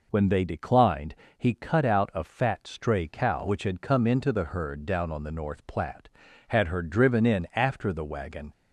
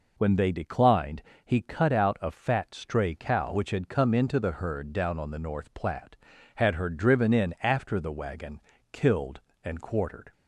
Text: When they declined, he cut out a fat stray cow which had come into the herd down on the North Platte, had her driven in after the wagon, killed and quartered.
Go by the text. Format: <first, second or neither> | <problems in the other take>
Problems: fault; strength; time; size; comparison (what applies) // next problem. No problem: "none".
second | stops before "killed and quartered"; at 8.5 s